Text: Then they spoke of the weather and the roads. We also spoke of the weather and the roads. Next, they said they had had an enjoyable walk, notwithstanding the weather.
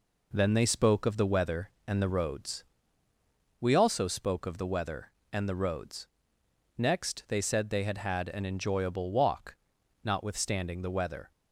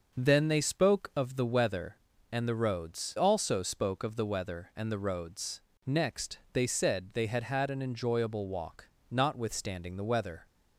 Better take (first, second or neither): first